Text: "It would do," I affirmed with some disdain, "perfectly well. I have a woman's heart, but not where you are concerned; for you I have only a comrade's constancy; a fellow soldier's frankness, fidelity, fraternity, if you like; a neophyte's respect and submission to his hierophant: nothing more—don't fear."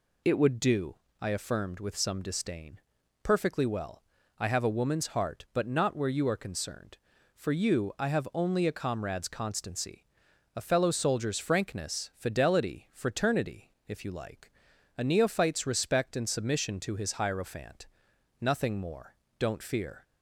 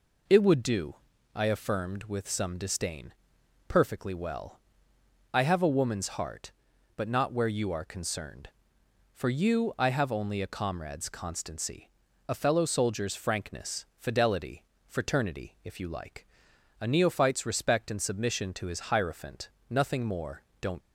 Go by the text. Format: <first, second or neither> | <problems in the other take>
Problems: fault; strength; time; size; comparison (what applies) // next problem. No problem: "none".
first | stops before "fear"; at 20.8 s